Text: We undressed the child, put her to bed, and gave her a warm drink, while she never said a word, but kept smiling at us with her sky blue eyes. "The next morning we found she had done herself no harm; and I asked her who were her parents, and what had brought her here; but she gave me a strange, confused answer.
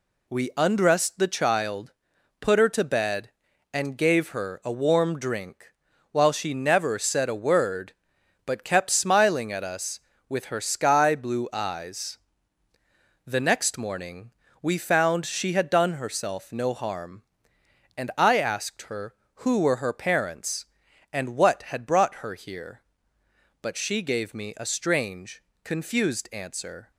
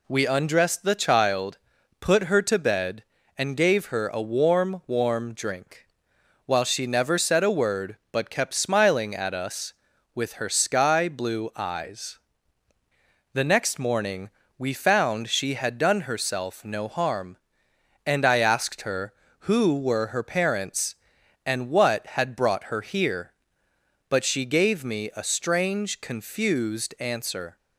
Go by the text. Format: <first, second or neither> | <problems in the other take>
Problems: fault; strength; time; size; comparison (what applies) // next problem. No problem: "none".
first | says "warm" twice; at 4.8 s // pauses between "morning" and "we"; slight; at 14.3 s; 0.26 s long; slight in the first